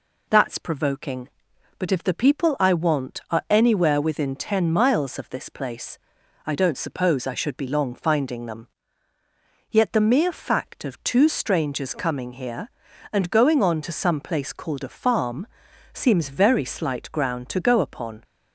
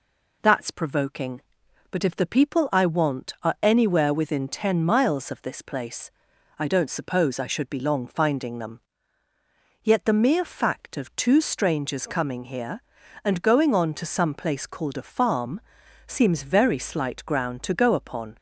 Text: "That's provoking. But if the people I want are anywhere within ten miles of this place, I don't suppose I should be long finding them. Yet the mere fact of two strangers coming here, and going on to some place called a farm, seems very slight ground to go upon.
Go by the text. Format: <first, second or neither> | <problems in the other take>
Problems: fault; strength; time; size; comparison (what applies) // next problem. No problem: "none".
neither | none